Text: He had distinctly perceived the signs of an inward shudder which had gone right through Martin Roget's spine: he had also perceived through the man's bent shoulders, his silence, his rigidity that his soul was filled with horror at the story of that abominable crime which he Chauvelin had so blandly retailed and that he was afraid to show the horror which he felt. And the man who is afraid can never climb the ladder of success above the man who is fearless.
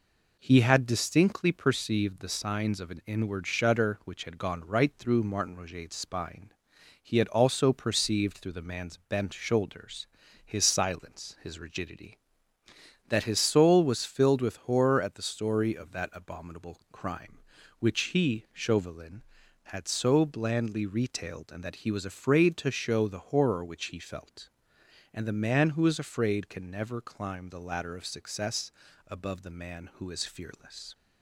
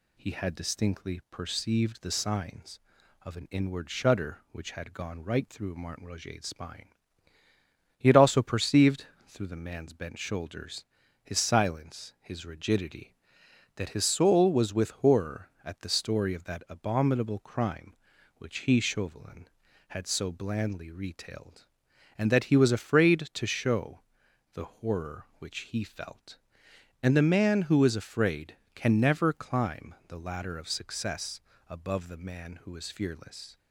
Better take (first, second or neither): first